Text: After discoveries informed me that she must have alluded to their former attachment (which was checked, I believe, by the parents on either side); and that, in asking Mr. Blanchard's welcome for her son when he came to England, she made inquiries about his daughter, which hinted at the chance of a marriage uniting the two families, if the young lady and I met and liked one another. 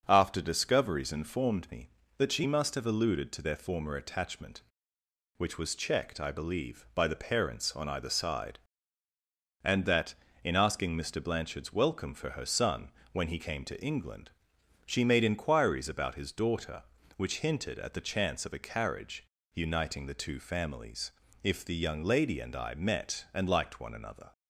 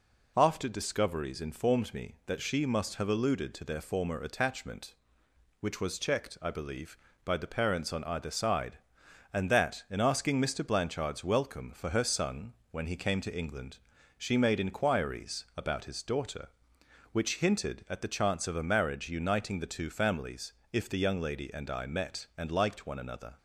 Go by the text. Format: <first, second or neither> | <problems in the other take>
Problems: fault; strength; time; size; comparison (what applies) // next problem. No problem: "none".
second | starts louder than the rest; until 1.0 s; 6.5 dB // pauses between "son" and "when"; slight; at 12.8 s; 0.22 s long; slight in the second // says "carriage" for "marriage"; at 18.5 s